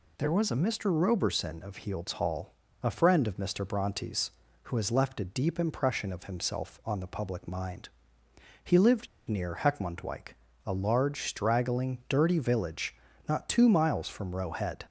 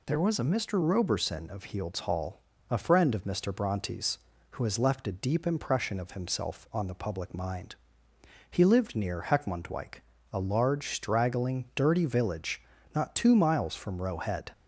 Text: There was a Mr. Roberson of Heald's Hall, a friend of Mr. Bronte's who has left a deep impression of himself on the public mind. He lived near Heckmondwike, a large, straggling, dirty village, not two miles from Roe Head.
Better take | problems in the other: second | pauses between "lived" and "near"; slight; at 9.0 s; 0.22 s long

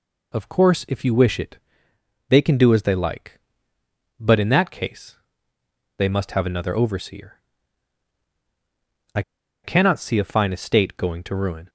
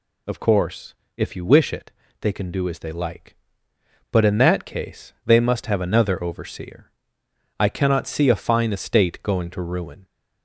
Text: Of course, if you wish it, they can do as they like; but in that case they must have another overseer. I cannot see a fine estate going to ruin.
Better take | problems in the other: second | pauses between "case" and "they"; noticeable; at 5.1 s; 0.82 s long // pauses between "I" and "cannot"; at 9.2 s; 0.43 s long

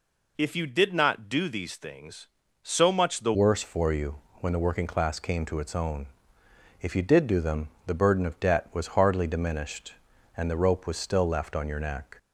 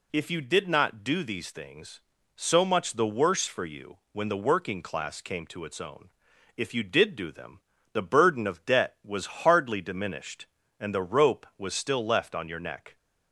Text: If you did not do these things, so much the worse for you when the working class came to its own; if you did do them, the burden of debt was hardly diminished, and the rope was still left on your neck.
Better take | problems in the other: second | changes voice at "worse"; from 3.3 s on; 8.8 s long // pauses between "you" and "when"; slight; at 4.1 s; 0.26 s long

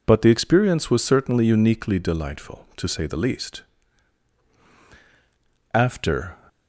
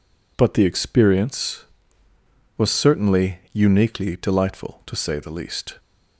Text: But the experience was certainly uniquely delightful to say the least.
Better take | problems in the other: second | goes on to say "After"; noticeable; from 5.7 s on; 0.64 s long

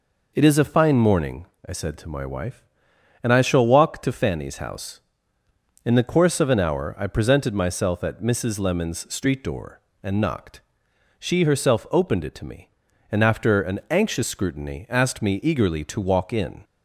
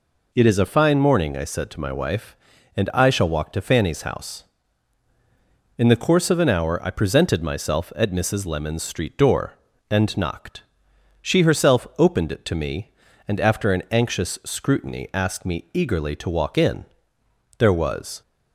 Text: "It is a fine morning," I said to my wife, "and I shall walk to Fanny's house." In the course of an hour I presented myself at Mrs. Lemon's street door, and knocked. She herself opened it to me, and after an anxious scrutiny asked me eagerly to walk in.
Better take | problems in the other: first | goes on to say "There was"; noticeable; from 17.5 s on; 0.64 s long

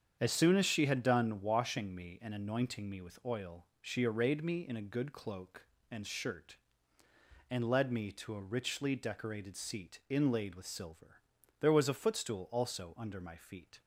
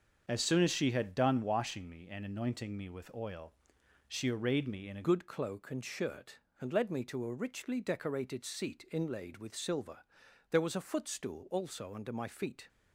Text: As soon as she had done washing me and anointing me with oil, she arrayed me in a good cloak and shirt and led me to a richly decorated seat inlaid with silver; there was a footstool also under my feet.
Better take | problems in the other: first | starts louder than the rest; until 1.2 s; 6.5 dB; strong in the first // changes voice at "good"; from 5.0 s on; 7.6 s long

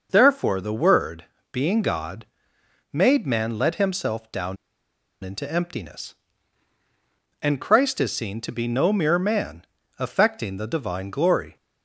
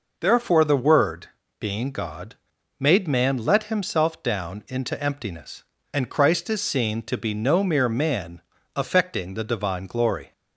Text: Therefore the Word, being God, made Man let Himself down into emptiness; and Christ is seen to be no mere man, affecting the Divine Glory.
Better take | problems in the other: second | pauses between "down" and "into"; noticeable; at 4.5 s; 0.67 s long

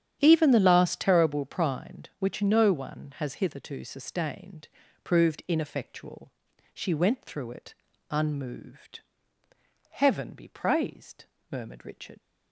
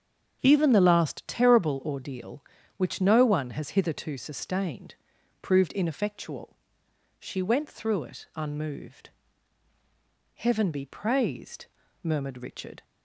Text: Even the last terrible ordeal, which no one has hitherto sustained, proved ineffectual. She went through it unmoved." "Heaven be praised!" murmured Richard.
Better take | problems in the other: second | starts louder than the rest; strong; until 1.2 s; 9.5 dB; also in the second // says "prind" for "ordeal"; at 1.4 s // pauses between "it" and "unmoved"; at 7.7 s; 0.38 s long

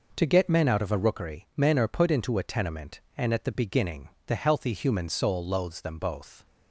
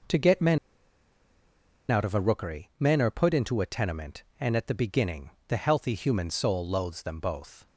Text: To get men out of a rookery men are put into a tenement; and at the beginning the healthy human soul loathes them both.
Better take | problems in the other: first | pauses between "men" and "out"; strong; at 0.5 s; 1.3 s long // pauses between "beginning" and "the"; slight; at 5.3 s; 0.18 s long; slight in the first

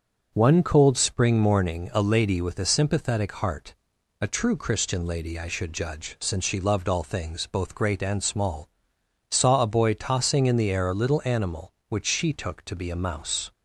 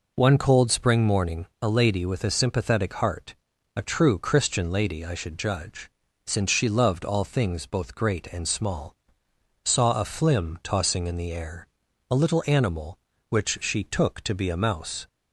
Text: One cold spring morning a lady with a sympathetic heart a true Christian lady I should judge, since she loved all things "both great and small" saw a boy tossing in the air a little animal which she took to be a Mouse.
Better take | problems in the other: first | pauses between "heart" and "a"; at 3.3 s; 0.42 s long; also in the first // pauses between "small" and "saw"; noticeable; at 8.9 s; 0.72 s long; noticeable in the first // says "flim" for "boy"; at 10.0 s // pauses between "air" and "a"; noticeable; at 11.6 s; 0.46 s long

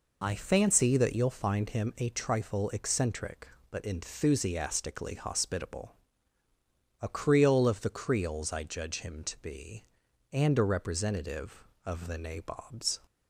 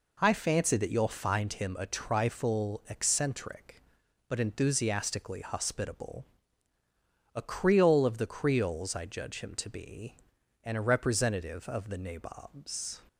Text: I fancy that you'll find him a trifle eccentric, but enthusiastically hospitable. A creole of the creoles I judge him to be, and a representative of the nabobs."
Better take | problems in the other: neither | none

